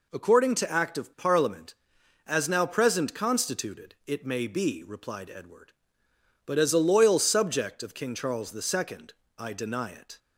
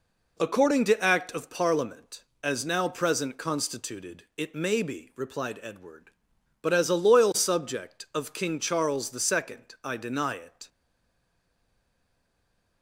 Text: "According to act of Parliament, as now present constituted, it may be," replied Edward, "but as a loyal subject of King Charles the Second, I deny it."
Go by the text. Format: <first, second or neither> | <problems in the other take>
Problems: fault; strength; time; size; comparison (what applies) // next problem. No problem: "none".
first | stays silent after the last word; from 10.6 s on; 2.2 s long